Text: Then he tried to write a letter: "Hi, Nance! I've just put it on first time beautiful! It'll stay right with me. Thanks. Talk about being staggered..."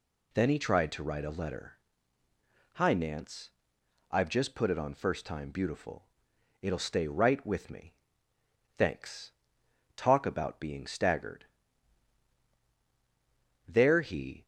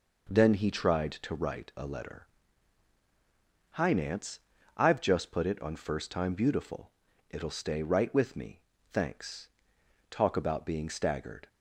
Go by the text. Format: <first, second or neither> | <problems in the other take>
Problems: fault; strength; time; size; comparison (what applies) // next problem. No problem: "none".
second | goes on to say "There he"; noticeable; from 13.6 s on; 0.78 s long